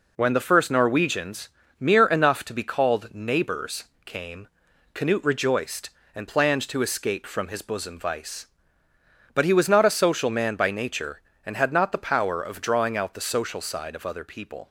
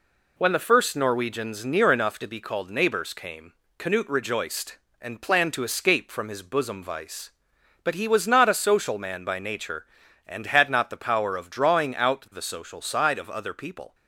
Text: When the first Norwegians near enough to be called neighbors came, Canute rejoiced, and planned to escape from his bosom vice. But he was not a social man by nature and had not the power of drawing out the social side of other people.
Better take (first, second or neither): second